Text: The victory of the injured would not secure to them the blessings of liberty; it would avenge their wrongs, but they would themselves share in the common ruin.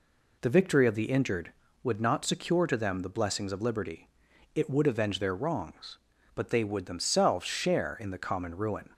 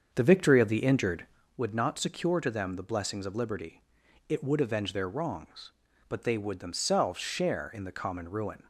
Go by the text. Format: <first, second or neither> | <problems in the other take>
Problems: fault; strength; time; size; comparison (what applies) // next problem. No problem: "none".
first | starts louder than the rest; until 1.5 s; 7 dB